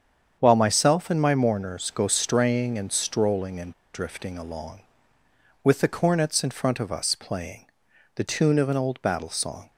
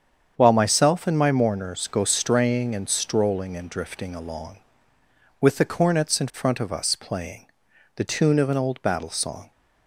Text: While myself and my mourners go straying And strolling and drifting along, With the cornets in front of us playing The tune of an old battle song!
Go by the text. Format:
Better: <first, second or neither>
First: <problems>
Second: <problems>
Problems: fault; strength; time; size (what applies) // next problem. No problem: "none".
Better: second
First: starts louder than the rest; strong; until 1.4 s; 7.5 dB // pauses between "and" and "drifting"; slight; at 3.7 s; 0.20 s long // pauses between "playing" and "The"; noticeable; at 7.6 s; 0.50 s long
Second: starts louder than the rest; strong; until 1.3 s; 7.5 dB // pauses between "playing" and "The"; noticeable; at 7.4 s; 0.50 s long